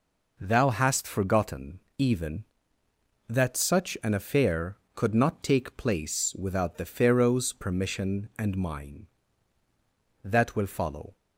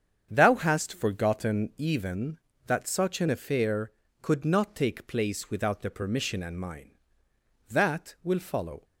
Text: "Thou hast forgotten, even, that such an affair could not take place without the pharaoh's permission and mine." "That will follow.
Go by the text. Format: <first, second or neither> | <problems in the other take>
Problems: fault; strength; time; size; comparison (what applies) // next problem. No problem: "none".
first | starts louder than the rest; strong; until 1.3 s; 8 dB // skips "pharaoh's"; at 5.8 s